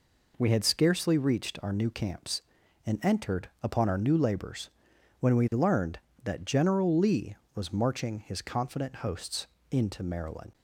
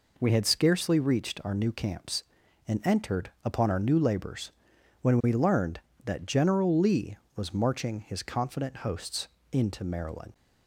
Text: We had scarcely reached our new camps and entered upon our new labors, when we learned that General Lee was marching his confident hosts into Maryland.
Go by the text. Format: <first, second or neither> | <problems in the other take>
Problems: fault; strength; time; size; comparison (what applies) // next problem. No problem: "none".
neither | pauses between "hosts" and "into"; slight; the same in both